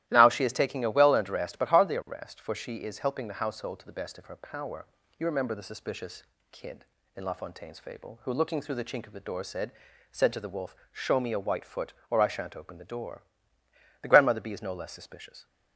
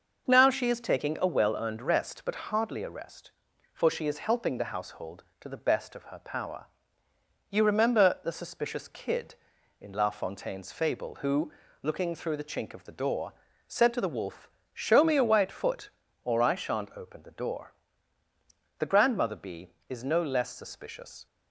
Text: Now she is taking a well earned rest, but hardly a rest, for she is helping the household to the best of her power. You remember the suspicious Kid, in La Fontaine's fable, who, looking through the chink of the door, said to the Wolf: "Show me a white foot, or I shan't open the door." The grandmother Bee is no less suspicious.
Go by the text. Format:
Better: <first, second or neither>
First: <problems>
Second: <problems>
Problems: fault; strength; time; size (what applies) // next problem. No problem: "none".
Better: second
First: starts louder than the rest; strong; until 1.0 s; 14.5 dB // pauses between "suspicious" and "Kid"; slight; at 6.2 s; 0.28 s long // says "said" twice; at 10.1 s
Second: none